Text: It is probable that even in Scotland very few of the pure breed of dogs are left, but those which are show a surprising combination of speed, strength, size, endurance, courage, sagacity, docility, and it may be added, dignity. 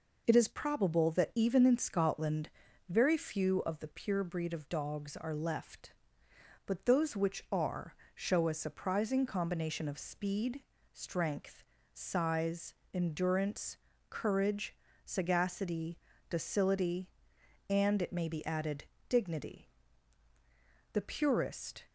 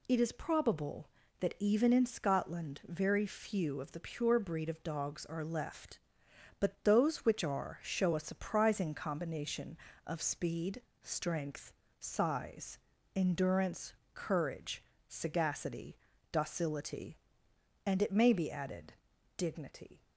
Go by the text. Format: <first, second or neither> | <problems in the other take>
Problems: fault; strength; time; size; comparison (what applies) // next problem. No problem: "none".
second | pauses between "Scotland" and "very"; at 2.4 s; 0.38 s long // pauses between "are" and "show"; slight; at 7.9 s; 0.20 s long // goes on to say "The purest"; noticeable; from 20.9 s on; 0.90 s long